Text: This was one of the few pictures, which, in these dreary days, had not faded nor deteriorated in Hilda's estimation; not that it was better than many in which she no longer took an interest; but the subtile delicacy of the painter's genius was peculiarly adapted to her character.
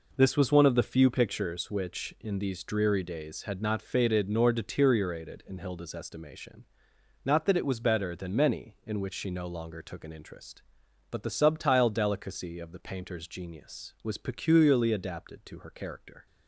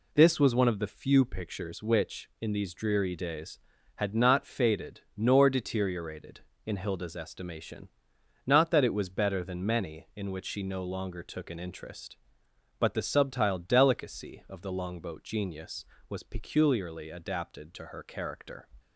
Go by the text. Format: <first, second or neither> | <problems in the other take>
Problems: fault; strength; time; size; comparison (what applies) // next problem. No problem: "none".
first | pauses between "faded" and "nor"; slight; at 4.9 s; 0.16 s long // says "longboat" for "painter's"; at 14.7 s